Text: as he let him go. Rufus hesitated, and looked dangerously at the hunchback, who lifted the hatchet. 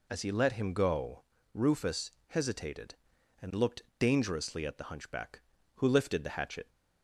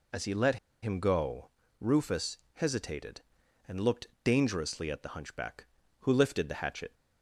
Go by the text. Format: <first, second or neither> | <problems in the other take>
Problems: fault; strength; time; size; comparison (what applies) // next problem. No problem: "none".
first | pauses between "let" and "him"; slight; at 0.5 s; 0.26 s long // pauses between "Rufus" and "hesitated"; slight; at 2.3 s; 0.18 s long; slight in the first // pauses between "looked" and "dangerously"; slight; at 4.0 s; 0.16 s long; slight in the first